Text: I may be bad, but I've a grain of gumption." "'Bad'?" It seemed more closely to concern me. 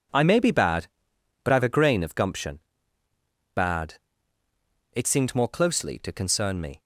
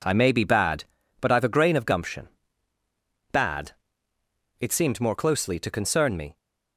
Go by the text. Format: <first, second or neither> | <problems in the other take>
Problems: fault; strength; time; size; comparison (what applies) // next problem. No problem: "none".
neither | none